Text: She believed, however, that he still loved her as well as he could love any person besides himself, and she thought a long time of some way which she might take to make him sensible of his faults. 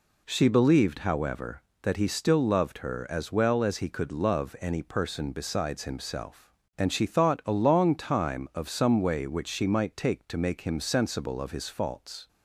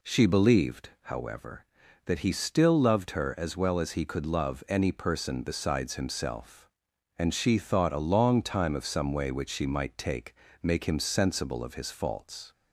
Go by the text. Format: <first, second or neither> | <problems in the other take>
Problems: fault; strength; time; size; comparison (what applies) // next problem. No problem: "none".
first | skips "to"; at 10.4 s